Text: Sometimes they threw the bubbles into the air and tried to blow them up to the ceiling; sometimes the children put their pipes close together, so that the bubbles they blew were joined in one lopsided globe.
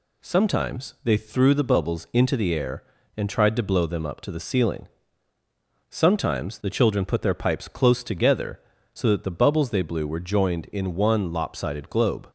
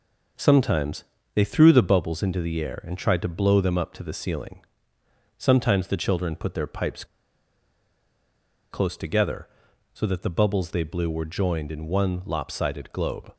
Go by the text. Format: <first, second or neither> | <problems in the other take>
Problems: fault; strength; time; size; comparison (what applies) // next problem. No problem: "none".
first | pauses between "Sometimes" and "they"; slight; at 1.0 s; 0.30 s long // pauses between "pipes" and "close"; strong; at 7.0 s; 1.6 s long